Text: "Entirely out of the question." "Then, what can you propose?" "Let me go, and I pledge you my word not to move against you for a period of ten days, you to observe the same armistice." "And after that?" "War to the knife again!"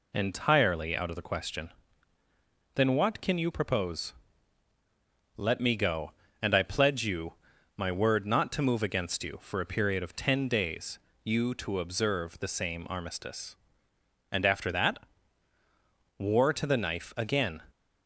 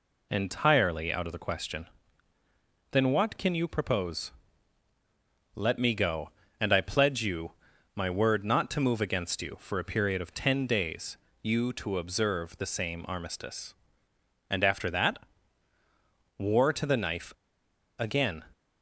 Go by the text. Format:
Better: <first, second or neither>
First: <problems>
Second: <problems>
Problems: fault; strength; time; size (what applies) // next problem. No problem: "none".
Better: first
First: pauses between "you" and "my"; at 7.3 s; 0.42 s long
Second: pauses between "you" and "my"; at 7.5 s; 0.42 s long // pauses between "knife" and "again"; noticeable; at 17.3 s; 0.65 s long